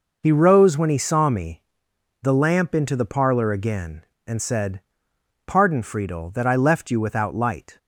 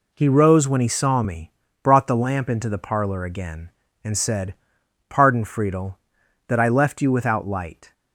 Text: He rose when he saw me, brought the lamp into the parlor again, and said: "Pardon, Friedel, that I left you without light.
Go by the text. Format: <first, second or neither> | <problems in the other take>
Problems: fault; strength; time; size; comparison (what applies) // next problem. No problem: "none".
second | skips "brought"; at 1.9 s